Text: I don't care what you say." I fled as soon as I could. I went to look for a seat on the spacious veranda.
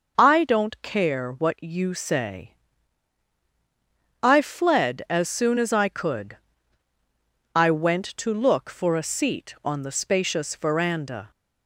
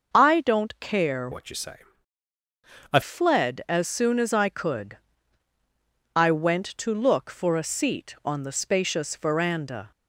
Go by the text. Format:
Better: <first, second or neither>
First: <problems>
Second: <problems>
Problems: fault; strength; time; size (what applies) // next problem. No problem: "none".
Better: first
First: starts louder than the rest; noticeable; until 1.1 s; 6 dB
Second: starts louder than the rest; noticeable; until 1.1 s; 6 dB // changes voice from "what" to "I"; from 1.3 to 3.0 s; 1.7 s long